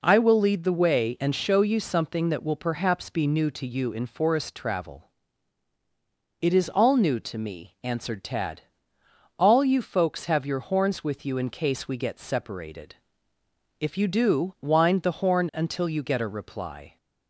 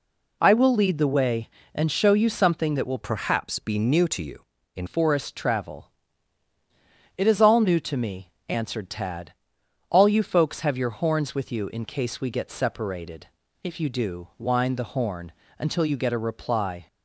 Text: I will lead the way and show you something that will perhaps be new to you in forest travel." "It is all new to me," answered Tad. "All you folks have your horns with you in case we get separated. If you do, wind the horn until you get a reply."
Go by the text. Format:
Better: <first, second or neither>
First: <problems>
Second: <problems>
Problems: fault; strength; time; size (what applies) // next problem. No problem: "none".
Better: first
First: none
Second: changes voice from "perhaps" to "in"; from 3.0 to 4.8 s; 1.8 s long // pauses between "horn" and "until"; slight; at 15.3 s; 0.28 s long